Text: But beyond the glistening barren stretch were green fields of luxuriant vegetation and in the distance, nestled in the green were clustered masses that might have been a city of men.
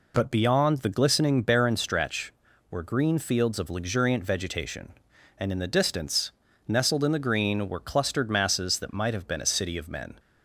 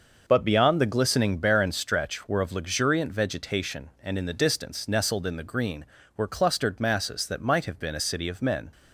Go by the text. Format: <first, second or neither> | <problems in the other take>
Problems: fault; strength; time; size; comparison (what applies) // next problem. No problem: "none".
first | starts louder than the rest; noticeable; until 1.2 s; 6 dB // skips "green fields"; at 2.4 s